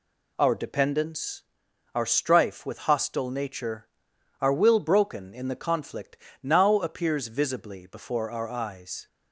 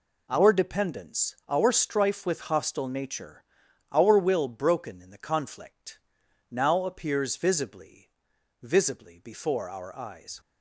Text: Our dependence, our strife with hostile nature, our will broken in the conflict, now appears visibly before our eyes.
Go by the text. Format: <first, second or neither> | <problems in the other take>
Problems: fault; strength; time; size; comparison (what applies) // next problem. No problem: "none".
first | says "visibly" twice; at 8.6 s